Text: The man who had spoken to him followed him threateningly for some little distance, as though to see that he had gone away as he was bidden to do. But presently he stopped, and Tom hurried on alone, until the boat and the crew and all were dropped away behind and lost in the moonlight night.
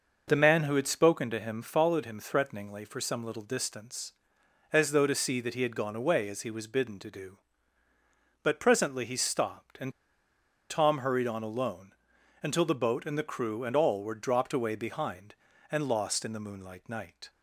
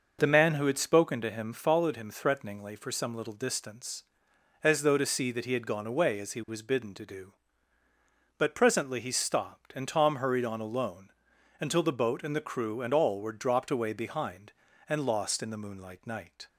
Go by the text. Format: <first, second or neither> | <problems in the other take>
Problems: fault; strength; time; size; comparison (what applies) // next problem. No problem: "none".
second | pauses between "and" and "Tom"; noticeable; at 9.9 s; 0.79 s long